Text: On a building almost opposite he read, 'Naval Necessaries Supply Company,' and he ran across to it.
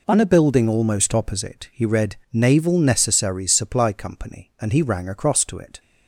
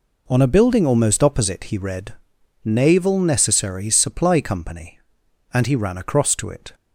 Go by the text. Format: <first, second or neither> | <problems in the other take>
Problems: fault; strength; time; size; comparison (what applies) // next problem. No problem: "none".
second | says "rang" for "ran"; at 4.8 s